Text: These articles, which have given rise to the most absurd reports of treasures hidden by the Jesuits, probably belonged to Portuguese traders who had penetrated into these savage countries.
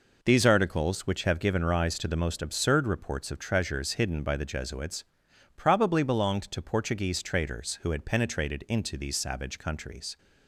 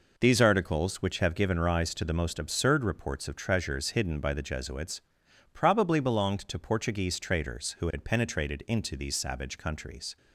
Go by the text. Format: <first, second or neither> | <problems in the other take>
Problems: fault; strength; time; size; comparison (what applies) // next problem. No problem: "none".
neither | none